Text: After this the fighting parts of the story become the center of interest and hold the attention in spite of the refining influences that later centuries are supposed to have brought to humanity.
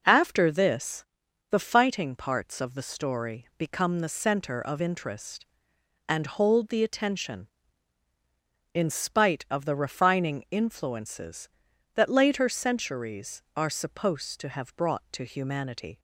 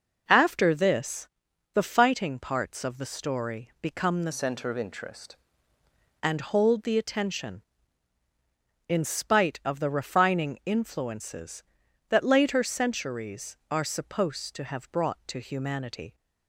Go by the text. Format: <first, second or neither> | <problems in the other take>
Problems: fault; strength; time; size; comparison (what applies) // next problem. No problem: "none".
first | pauses between "this" and "the"; noticeable; at 1.2 s; 0.46 s long; noticeable in the first // changes voice from "center" to "interest"; from 4.3 to 5.3 s; 1.0 s long